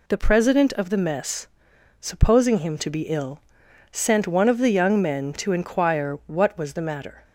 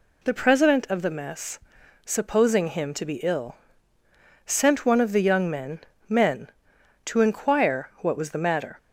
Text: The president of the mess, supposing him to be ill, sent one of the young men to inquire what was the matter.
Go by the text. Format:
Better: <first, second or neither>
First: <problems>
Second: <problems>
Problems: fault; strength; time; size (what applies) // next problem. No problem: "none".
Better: first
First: none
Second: says "men" twice; at 6.0 s